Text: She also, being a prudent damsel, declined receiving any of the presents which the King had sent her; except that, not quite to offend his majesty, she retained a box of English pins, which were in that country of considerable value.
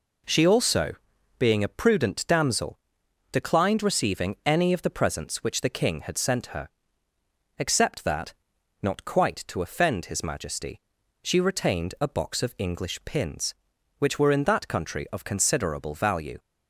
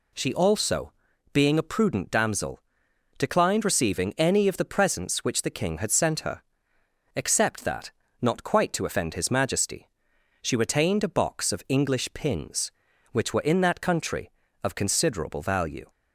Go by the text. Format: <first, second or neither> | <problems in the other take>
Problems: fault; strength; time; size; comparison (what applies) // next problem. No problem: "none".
neither | none